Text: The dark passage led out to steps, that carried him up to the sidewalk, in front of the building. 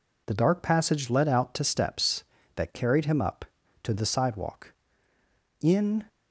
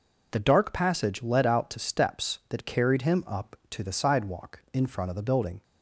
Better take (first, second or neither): second